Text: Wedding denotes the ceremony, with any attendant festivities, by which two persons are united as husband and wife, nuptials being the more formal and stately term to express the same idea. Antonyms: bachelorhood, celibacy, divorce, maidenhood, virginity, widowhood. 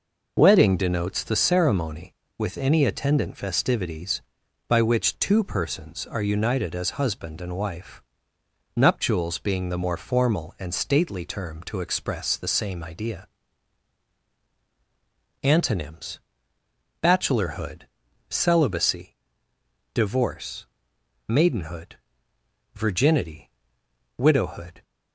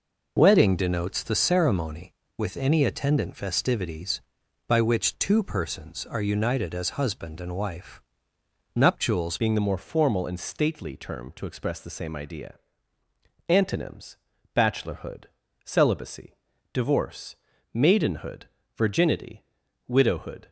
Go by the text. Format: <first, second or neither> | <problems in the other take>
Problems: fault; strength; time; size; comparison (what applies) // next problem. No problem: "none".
first | changes voice at "being"; from 9.3 s on; 11.1 s long